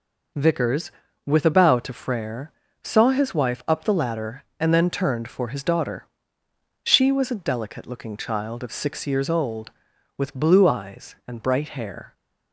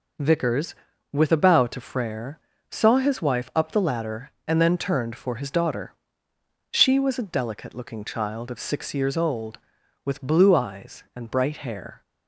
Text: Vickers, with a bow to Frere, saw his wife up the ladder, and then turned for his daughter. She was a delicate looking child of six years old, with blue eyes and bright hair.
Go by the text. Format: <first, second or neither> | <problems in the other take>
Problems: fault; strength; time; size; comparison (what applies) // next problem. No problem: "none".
neither | none